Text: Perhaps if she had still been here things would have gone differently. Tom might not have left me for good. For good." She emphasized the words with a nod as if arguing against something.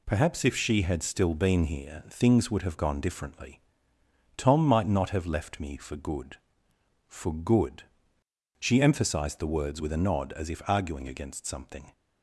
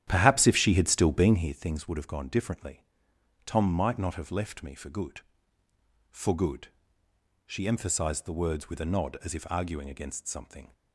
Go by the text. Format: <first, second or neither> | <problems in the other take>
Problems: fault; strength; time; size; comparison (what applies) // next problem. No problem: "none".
first | starts louder than the rest; strong; until 1.6 s; 11 dB